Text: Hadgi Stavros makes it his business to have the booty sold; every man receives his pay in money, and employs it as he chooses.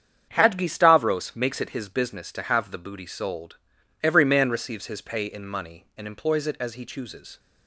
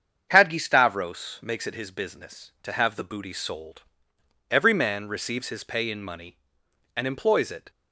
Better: first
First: starts louder than the rest; strong; until 1.3 s; 8 dB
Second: starts louder than the rest; strong; until 1.3 s; 7.5 dB // stops before "as he chooses"; at 7.6 s

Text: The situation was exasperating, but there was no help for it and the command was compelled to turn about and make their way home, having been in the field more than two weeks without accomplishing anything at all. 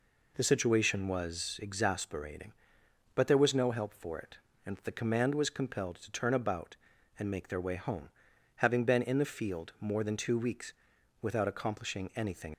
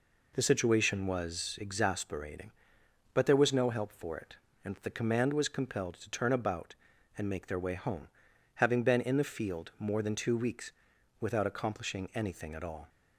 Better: second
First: pauses between "weeks" and "without"; noticeable; at 10.7 s; 0.48 s long // stops before "at all"; at 12.5 s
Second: pauses between "weeks" and "without"; noticeable; at 10.7 s; 0.48 s long

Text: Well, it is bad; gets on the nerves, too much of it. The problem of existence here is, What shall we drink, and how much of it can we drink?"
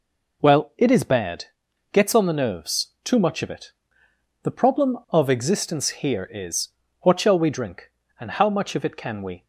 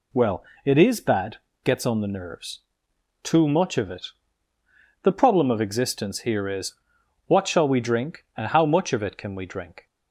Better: second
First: stops before "drink"; at 9.4 s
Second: none

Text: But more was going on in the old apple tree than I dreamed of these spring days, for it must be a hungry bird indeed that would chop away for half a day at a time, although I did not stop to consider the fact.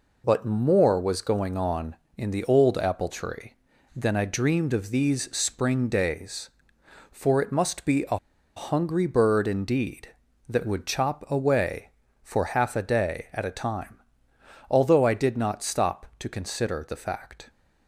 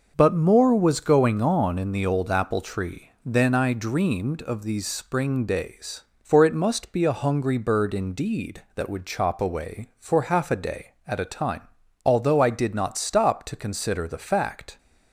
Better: second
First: pauses between "a" and "hungry"; at 8.1 s; 0.39 s long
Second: none

